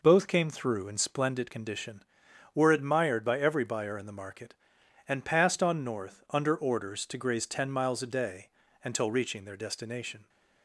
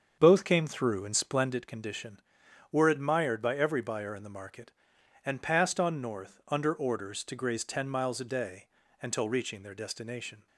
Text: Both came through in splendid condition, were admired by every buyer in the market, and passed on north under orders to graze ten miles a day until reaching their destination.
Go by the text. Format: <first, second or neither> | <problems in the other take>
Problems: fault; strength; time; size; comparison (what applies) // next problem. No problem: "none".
first | starts louder than the rest; until 1.6 s; 7 dB // pauses between "day" and "until"; at 8.6 s; 0.38 s long; also in the first